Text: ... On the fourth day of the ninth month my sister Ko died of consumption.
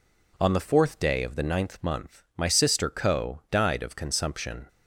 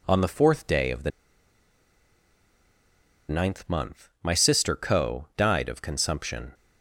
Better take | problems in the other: first | pauses between "the" and "ninth"; strong; at 1.1 s; 2.1 s long

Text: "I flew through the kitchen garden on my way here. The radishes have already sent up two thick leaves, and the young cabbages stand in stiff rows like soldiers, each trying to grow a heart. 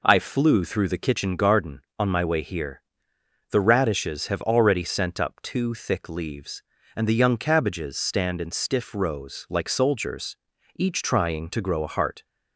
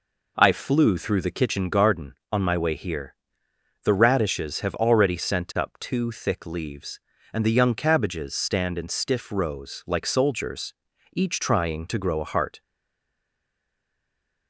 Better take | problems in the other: first | stays silent after the last word; noticeable; from 12.6 s on; 1.8 s long

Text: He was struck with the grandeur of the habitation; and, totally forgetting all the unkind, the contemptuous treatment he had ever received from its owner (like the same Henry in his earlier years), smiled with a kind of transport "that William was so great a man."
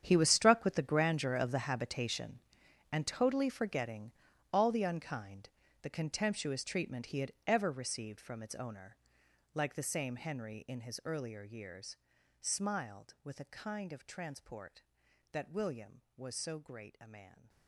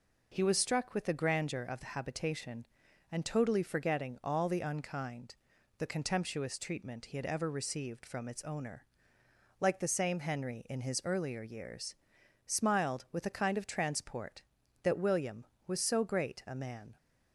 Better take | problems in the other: second | gets quieter; strong; throughout; 16 dB // pauses between "forgetting" and "all"; at 4.1 s; 0.40 s long

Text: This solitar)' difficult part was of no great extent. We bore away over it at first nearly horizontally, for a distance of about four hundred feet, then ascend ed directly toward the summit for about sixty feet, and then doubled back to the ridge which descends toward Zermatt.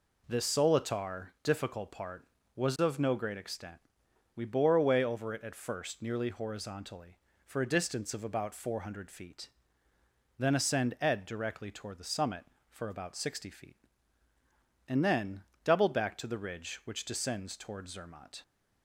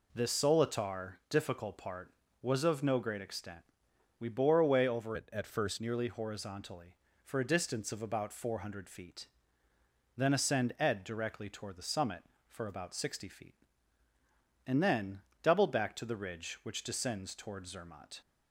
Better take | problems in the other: first | changes voice from "it" to "first"; from 5.1 to 5.7 s; 0.6 s long // pauses between "then" and "doubled"; slight; at 15.2 s; 0.20 s long; slight in the first

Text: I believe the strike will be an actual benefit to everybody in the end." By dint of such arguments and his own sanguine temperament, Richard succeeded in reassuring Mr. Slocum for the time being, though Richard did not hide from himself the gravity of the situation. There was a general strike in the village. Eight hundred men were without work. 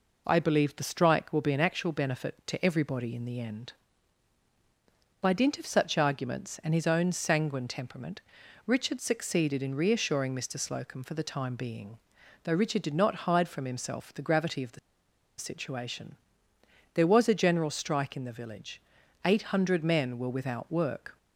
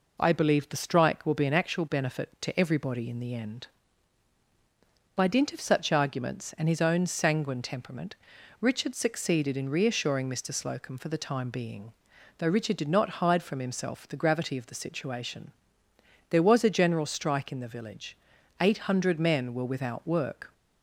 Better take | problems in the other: second | pauses between "the" and "situation"; noticeable; at 14.7 s; 0.59 s long

